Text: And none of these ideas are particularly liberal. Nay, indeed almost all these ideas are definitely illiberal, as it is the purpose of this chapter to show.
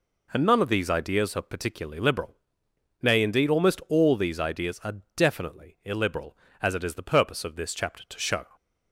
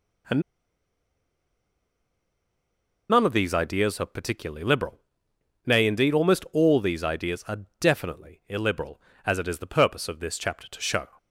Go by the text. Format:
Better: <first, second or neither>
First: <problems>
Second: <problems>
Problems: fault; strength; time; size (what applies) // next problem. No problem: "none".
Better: first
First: pauses between "are" and "definitely"; slight; at 4.9 s; 0.18 s long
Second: pauses between "And" and "none"; strong; at 0.4 s; 2.6 s long // pauses between "are" and "definitely"; slight; at 7.6 s; 0.18 s long